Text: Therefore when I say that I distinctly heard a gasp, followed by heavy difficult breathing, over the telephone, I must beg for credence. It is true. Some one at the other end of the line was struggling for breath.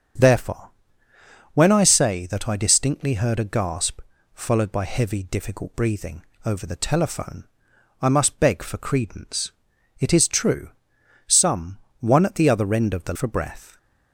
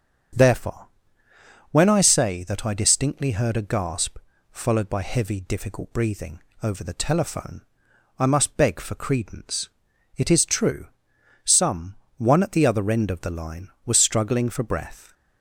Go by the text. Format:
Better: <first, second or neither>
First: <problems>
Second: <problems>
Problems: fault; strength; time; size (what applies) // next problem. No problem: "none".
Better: second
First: starts louder than the rest; strong; until 2.0 s; 7.5 dB // pauses between "Therefore" and "when"; noticeable; at 0.7 s; 0.84 s long // pauses between "Some" and "one"; slight; at 11.7 s; 0.22 s long // skips "line was struggling"; at 13.1 s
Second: starts louder than the rest; strong; until 2.2 s; 7.5 dB // pauses between "Therefore" and "when"; noticeable; at 0.8 s; 0.84 s long // pauses between "Some" and "one"; slight; at 11.9 s; 0.22 s long